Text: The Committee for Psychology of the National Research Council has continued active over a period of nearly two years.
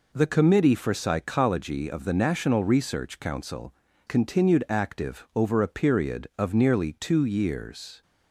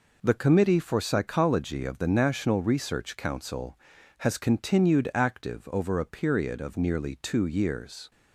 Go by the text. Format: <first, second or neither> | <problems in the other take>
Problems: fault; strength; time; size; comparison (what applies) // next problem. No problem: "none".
second | skips "has"; at 3.8 s